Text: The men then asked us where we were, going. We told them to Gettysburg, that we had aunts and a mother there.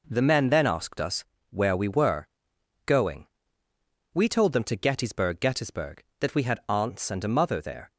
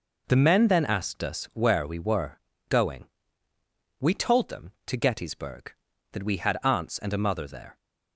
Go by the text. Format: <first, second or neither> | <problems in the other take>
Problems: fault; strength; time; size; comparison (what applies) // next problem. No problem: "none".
second | pauses between "us" and "where"; slight; at 1.2 s; 0.26 s long // says "Gettysburg" twice; at 5.3 s